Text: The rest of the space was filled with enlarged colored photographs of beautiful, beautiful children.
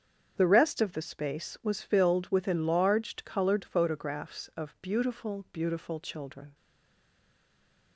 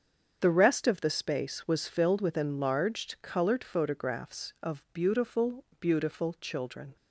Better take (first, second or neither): second